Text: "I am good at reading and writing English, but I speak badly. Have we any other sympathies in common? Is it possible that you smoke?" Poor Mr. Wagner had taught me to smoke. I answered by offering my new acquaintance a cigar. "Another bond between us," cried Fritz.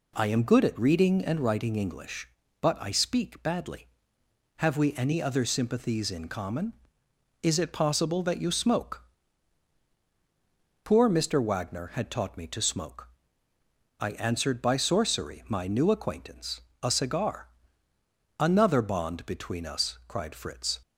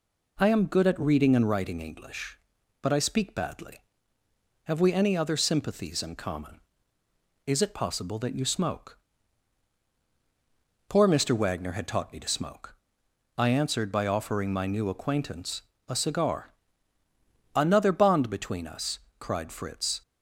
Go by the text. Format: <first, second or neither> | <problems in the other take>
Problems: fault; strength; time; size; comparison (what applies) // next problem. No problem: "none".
second | says "sorcery" for "offering"; at 14.7 s // pauses between "acquaintance" and "a"; slight; at 16.6 s; 0.22 s long; slight in the second